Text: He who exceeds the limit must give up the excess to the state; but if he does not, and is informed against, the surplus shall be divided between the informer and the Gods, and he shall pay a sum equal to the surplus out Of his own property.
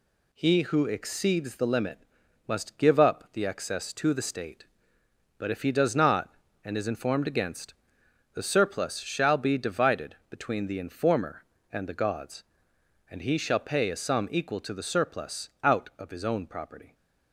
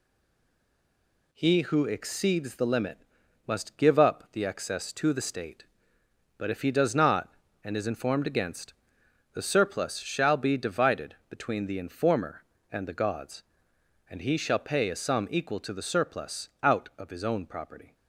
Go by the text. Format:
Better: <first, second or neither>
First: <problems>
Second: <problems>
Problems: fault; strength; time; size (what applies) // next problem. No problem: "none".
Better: first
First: pauses between "limit" and "must"; noticeable; at 1.9 s; 0.48 s long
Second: stays silent before the first word; noticeable; until 1.3 s; 1.3 s long // pauses between "limit" and "must"; noticeable; at 2.9 s; 0.48 s long